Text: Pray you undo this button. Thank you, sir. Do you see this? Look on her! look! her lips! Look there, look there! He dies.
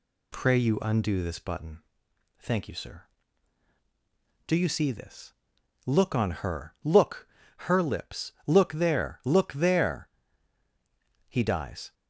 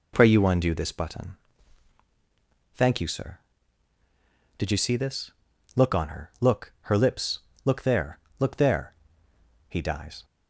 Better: first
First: none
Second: says "Did" for "Do"; at 4.5 s

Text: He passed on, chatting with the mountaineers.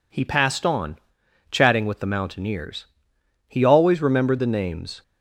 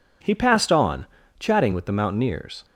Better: second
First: goes on to say "He always remembered the names"; from 3.4 s on; 1.5 s long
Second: none

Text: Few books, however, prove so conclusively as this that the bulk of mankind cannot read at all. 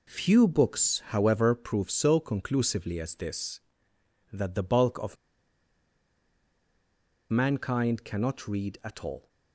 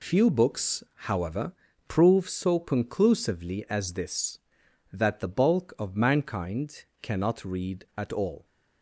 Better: second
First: pauses between "of" and "mankind"; strong; at 5.1 s; 2.1 s long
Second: none

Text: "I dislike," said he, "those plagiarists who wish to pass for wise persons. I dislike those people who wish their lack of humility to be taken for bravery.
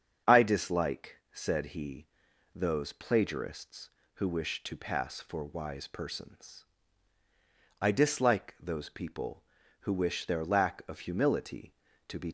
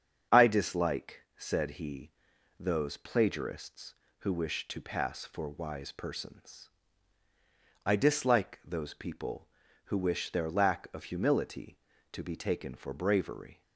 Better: second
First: starts louder than the rest; strong; until 1.4 s; 7 dB // stops before "taken for bravery"; at 12.2 s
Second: starts louder than the rest; strong; until 1.4 s; 7 dB

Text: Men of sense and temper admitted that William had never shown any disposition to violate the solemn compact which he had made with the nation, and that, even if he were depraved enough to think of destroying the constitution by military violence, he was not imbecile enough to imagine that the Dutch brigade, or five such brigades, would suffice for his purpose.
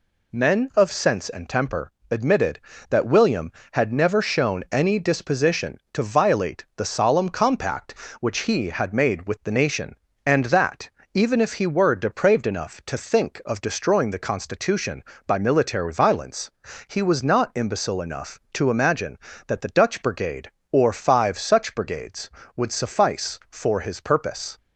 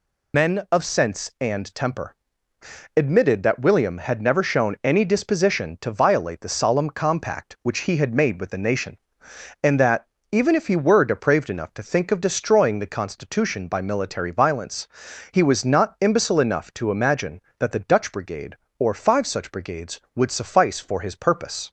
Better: first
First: pauses between "temper" and "admitted"; slight; at 1.8 s; 0.22 s long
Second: loses the start of "Men"; at 0.3 s; 70 ms // pauses between "temper" and "admitted"; noticeable; at 2.1 s; 0.80 s long

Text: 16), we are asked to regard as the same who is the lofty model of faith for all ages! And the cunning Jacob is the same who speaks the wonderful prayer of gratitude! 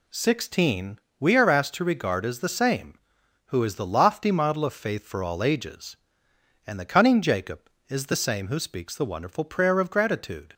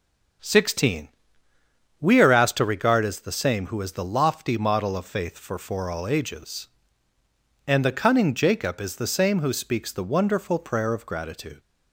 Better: first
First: none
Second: starts louder than the rest; until 2.3 s; 6.5 dB // says "for" twice; at 5.5 s

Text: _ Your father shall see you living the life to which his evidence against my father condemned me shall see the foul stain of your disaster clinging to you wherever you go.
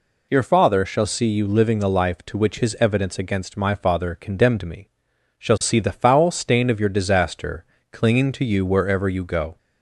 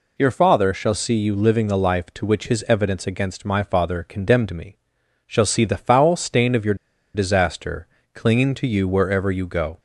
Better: first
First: pauses between "me" and "shall"; noticeable; at 4.8 s; 0.50 s long // pauses between "disaster" and "clinging"; slight; at 7.6 s; 0.26 s long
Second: pauses between "me" and "shall"; noticeable; at 4.7 s; 0.50 s long // pauses between "your" and "disaster"; at 6.7 s; 0.39 s long // pauses between "disaster" and "clinging"; slight; at 7.8 s; 0.26 s long

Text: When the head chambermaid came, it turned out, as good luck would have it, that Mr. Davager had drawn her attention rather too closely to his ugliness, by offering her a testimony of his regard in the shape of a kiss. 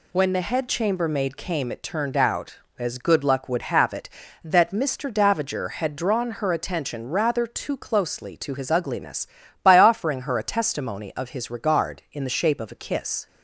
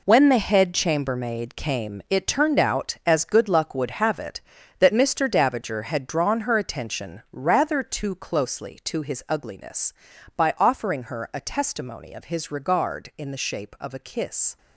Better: first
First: none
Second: gets quieter; strong; throughout; 10.5 dB

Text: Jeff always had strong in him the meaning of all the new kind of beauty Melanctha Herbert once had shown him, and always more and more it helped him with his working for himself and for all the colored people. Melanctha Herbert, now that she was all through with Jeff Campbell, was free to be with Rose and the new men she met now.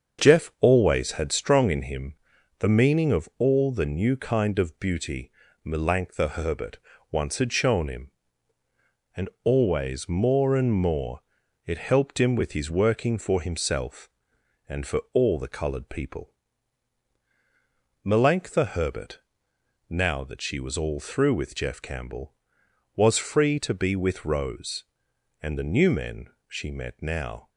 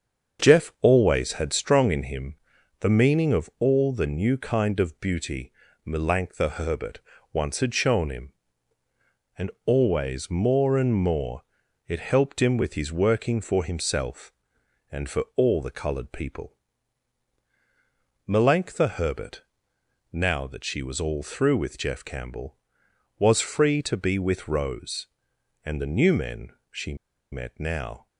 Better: first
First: starts louder than the rest; until 1.2 s; 7 dB // pauses between "him" and "the"; at 2.1 s; 0.44 s long // pauses between "beauty" and "Melanctha"; slight; at 5.3 s; 0.34 s long // pauses between "Herbert" and "once"; slight; at 6.7 s; 0.32 s long // pauses between "and" and "always"; slight; at 9.2 s; 0.16 s long // pauses between "more" and "it"; at 11.2 s; 0.44 s long // pauses between "men" and "she"; slight; at 26.2 s; 0.22 s long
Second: starts louder than the rest; until 1.4 s; 7 dB // pauses between "him" and "the"; at 2.3 s; 0.44 s long // pauses between "beauty" and "Melanctha"; slight; at 5.5 s; 0.34 s long // pauses between "Herbert" and "once"; slight; at 7.0 s; 0.32 s long // pauses between "and" and "always"; slight; at 9.5 s; 0.16 s long // pauses between "more" and "it"; at 11.4 s; 0.44 s long // pauses between "men" and "she"; slight; at 26.4 s; 0.22 s long // pauses between "she" and "met"; at 26.9 s; 0.37 s long

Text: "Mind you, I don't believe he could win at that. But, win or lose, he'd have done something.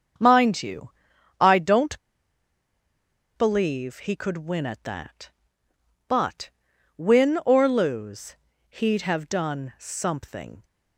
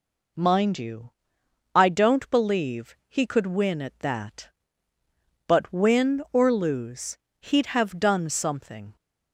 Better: second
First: starts louder than the rest; until 1.6 s; 7 dB // pauses between "don't" and "believe"; strong; at 1.9 s; 1.3 s long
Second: none

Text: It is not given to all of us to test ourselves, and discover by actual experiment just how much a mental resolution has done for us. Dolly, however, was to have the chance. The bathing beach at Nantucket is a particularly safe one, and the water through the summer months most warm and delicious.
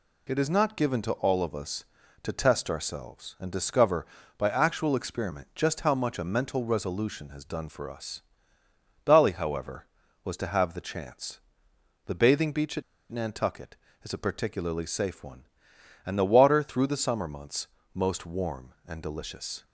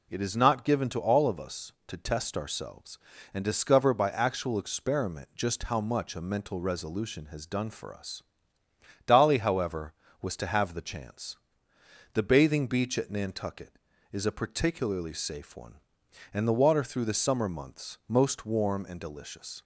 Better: second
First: pauses between "at" and "Nantucket"; slight; at 12.8 s; 0.28 s long // pauses between "months" and "most"; slight; at 17.6 s; 0.28 s long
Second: none

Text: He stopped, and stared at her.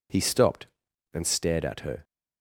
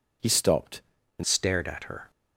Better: first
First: none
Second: changes voice at "stared"; from 1.2 s on; 0.9 s long

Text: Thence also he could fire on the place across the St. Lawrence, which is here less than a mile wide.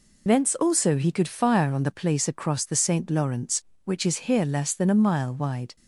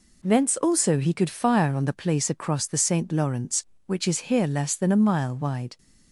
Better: second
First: loses the start of "Thence"; at 0.2 s; 45 ms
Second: none

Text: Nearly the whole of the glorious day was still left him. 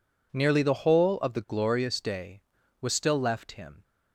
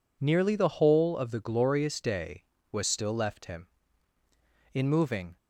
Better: first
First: none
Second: goes on to say "In moving"; noticeable; from 4.7 s on; 0.64 s long

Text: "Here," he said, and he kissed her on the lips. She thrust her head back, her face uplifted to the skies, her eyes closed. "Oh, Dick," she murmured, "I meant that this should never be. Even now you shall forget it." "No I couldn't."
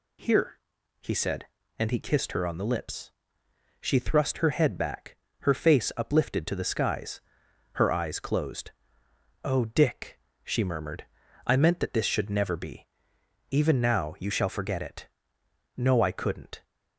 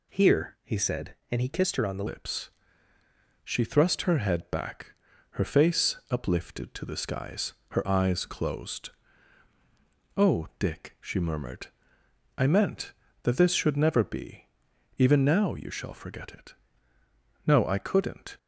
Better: first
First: none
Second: changes voice at "lips"; from 2.0 s on; 16.3 s long // pauses between "face" and "uplifted"; slight; at 5.9 s; 0.16 s long

